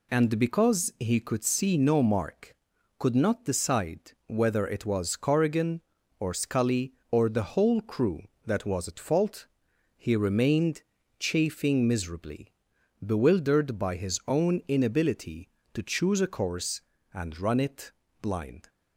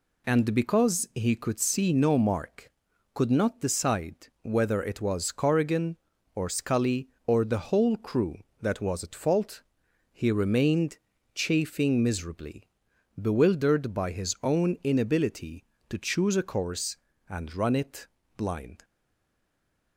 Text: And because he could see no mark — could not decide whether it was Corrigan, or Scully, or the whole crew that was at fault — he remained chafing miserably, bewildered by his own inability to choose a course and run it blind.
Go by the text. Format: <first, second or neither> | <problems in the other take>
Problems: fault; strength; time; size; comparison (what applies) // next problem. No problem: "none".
first | pauses between "remained" and "chafing"; slight; at 10.9 s; 0.36 s long; slight in the first // pauses between "it" and "blind"; slight; at 18.0 s; 0.30 s long; slight in the first // stays silent after the last word; from 18.8 s on; 1.1 s long